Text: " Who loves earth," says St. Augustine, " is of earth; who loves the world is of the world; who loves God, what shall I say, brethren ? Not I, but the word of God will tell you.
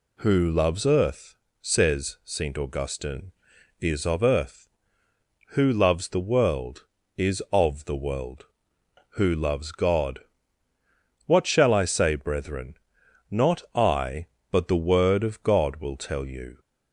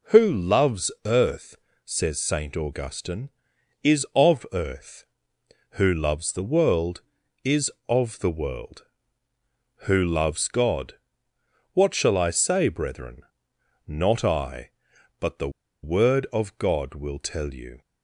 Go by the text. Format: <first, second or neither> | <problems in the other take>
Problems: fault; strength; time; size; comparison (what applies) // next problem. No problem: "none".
first | pauses between "the" and "word"; slight; at 15.4 s; 0.33 s long